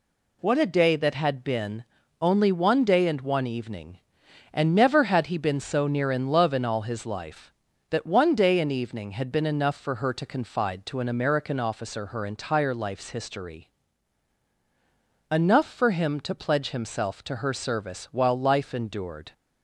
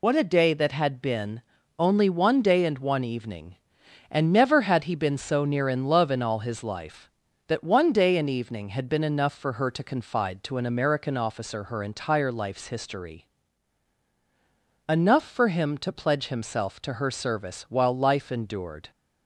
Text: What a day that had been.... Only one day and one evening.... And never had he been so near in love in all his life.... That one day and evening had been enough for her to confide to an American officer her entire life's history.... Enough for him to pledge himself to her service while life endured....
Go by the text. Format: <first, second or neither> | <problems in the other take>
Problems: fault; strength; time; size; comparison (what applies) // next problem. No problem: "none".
first | loses the start of "What"; at 0.0 s; 50 ms